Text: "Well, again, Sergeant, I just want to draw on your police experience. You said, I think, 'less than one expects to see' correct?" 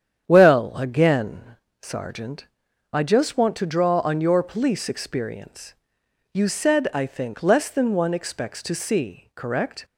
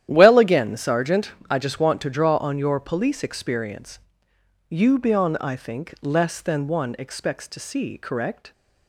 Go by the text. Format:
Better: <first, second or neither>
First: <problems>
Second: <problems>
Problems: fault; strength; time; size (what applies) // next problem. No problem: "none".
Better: first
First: starts louder than the rest; strong; until 1.2 s; 8.5 dB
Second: starts louder than the rest; strong; until 1.1 s; 11 dB // says "bion" for "said"; at 4.9 s